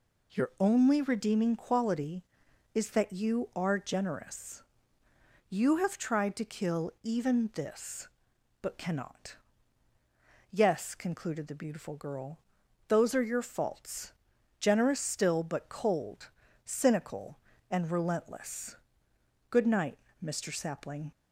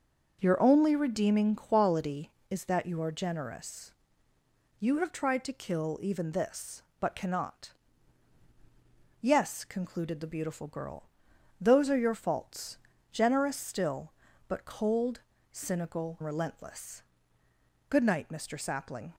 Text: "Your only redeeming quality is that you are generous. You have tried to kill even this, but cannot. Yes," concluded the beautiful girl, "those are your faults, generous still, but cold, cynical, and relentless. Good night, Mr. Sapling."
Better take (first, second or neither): first